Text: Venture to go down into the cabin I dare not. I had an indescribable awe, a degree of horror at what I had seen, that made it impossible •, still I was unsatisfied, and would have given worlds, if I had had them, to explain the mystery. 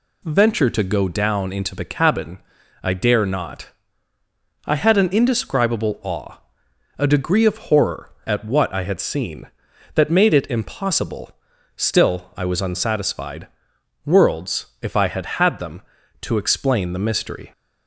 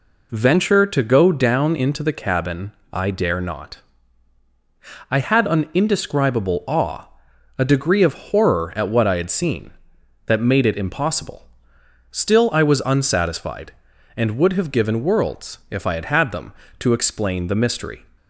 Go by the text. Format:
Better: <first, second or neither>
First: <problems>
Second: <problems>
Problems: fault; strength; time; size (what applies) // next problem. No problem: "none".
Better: second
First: pauses between "cabin" and "I"; at 2.3 s; 0.44 s long // skips "and would have given"; at 13.7 s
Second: pauses between "cabin" and "I"; slight; at 2.7 s; 0.22 s long